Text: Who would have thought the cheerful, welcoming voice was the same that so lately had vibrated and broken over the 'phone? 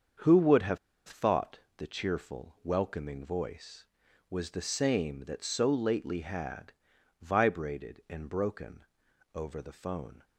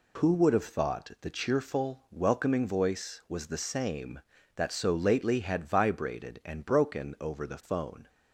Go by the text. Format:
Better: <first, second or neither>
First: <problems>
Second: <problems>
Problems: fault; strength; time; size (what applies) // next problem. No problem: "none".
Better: second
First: starts louder than the rest; until 1.4 s; 7 dB // pauses between "have" and "thought"; slight; at 0.7 s; 0.29 s long // pauses between "thought" and "the"; slight; at 1.5 s; 0.18 s long // pauses between "had" and "vibrated"; noticeable; at 6.7 s; 0.48 s long // pauses between "broken" and "over"; noticeable; at 8.8 s; 0.50 s long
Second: none